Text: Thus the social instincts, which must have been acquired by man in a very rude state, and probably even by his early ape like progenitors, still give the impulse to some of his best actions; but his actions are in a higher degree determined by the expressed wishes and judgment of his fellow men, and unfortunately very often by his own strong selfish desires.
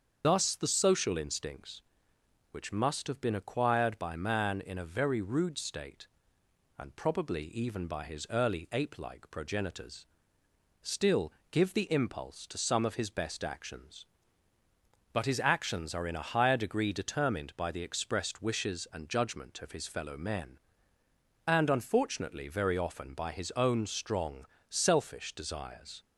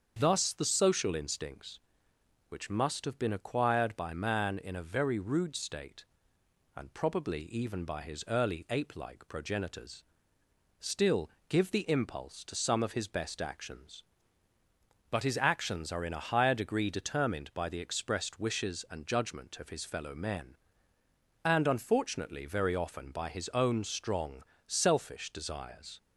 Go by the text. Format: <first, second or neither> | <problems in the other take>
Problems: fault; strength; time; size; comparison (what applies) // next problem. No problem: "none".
second | loses the start of "Thus"; at 0.2 s; 65 ms // starts louder than the rest; until 1.2 s; 7 dB; also in the second // pauses between "still" and "give"; slight; at 11.3 s; 0.20 s long; slight in the second // pauses between "strong" and "selfish"; slight; at 24.4 s; 0.22 s long; slight in the second